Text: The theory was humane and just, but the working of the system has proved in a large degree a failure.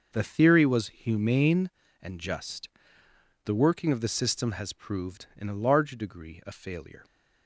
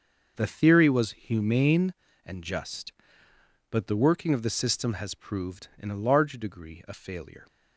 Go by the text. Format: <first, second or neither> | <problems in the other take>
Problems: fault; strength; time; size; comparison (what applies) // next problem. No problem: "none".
second | starts louder than the rest; noticeable; until 1.1 s; 6 dB; noticeable in the second // skips "but"; at 3.0 s